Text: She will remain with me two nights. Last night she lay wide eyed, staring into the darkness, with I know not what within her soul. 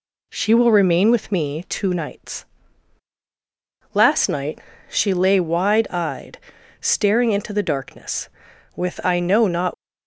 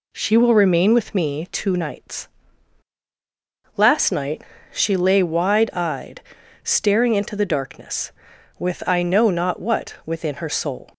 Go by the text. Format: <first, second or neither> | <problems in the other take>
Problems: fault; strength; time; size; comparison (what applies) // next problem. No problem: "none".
second | pauses between "night" and "she"; slight; at 4.5 s; 0.28 s long; slight in the second // stops before "what within her soul"; at 9.7 s